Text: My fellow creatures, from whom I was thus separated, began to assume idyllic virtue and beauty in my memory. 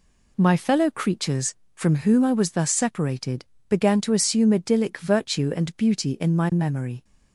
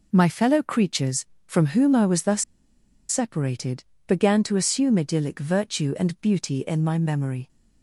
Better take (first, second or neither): first